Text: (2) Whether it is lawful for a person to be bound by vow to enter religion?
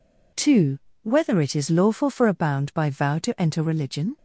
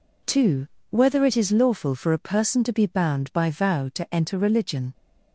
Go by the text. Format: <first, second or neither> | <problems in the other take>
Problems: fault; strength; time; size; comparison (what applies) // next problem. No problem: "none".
second | skips "person to be"; at 2.3 s